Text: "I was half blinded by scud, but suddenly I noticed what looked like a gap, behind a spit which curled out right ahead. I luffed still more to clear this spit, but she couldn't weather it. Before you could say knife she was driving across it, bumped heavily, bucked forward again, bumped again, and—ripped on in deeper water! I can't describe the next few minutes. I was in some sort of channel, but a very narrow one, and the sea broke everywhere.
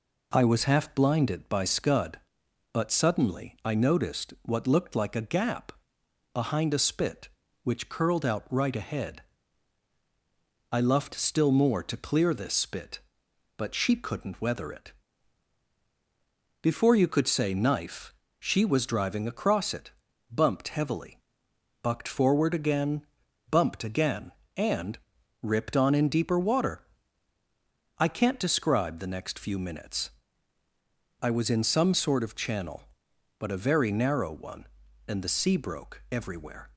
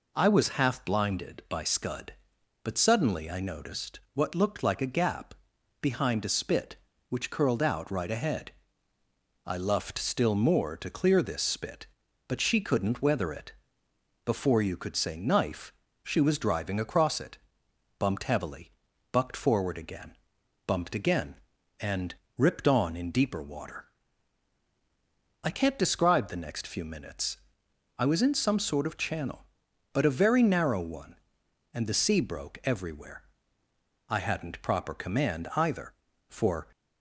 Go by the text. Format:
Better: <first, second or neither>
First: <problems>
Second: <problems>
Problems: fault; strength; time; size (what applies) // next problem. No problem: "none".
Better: first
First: pauses between "knife" and "she"; slight; at 18.1 s; 0.26 s long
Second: pauses between "noticed" and "what"; slight; at 3.9 s; 0.16 s long // pauses between "knife" and "she"; slight; at 15.7 s; 0.30 s long // goes on to say "I hadn't proper command either for"; strong; from 34.0 s on; 2.6 s long